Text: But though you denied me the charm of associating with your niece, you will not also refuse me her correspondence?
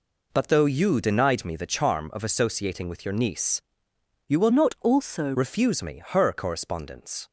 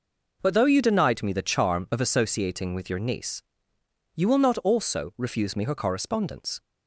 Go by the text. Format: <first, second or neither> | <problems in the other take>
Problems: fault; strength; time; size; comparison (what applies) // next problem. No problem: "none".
second | changes voice from "not" to "also"; from 4.5 to 5.3 s; 0.8 s long